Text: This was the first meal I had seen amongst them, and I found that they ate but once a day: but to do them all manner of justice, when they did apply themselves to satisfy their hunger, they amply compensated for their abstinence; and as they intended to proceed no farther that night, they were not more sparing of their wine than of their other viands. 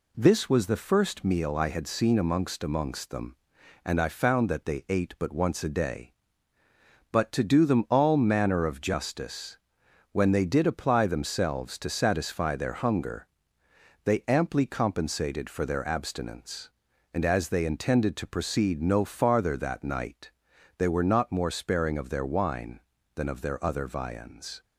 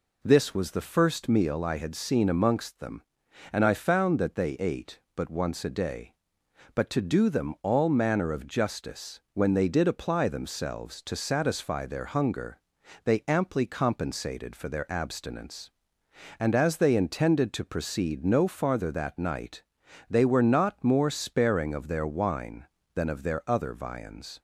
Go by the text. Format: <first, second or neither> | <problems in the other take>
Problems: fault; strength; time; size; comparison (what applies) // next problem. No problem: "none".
second | says "amongst" twice; at 2.6 s